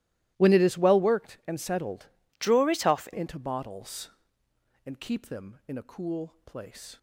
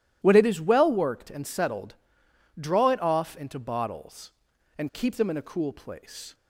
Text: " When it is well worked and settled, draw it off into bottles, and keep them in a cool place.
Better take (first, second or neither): second